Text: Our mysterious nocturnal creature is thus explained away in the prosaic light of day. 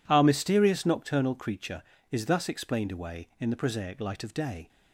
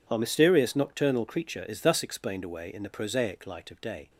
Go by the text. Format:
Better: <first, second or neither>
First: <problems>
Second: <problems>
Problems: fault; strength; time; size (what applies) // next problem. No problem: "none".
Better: neither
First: none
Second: none